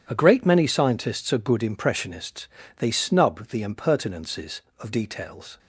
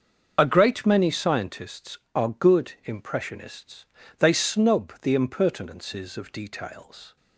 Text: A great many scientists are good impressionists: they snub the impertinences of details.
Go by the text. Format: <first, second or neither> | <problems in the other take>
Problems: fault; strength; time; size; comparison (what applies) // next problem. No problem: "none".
first | loses the start of "A"; at 0.3 s; 30 ms // starts louder than the rest; until 1.3 s; 6.5 dB